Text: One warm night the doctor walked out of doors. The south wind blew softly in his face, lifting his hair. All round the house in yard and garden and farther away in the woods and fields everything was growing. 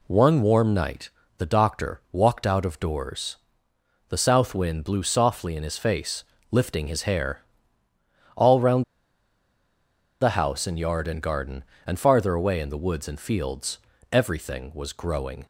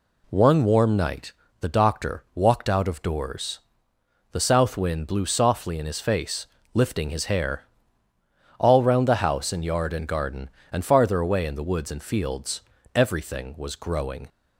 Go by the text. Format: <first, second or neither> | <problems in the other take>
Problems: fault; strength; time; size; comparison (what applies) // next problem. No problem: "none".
second | pauses between "night" and "the"; slight; at 1.1 s; 0.28 s long; slight in the second // pauses between "round" and "the"; strong; at 8.8 s; 1.3 s long // pauses between "fields" and "everything"; slight; at 13.7 s; 0.34 s long; slight in the second